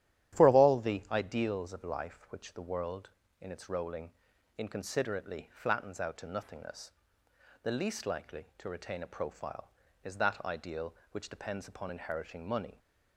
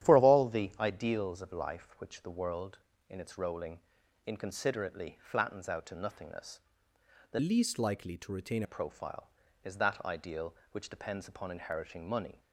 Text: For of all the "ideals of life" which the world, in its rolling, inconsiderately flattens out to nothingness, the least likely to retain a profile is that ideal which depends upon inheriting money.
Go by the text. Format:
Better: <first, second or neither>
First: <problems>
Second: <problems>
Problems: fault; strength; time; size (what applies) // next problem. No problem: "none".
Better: first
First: starts louder than the rest; strong; until 1.4 s; 11.5 dB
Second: starts louder than the rest; strong; until 1.1 s; 11 dB // changes voice from "least" to "retain"; from 7.4 to 8.6 s; 1.2 s long